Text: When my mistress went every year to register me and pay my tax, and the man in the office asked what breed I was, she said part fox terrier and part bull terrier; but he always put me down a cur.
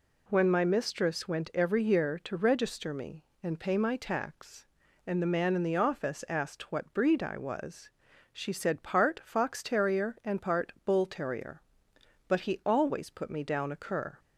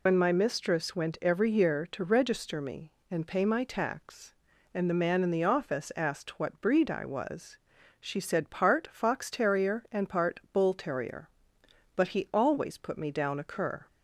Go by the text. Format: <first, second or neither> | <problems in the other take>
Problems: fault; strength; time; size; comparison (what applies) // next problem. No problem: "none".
first | loses the start of "When"; at 0.0 s; 100 ms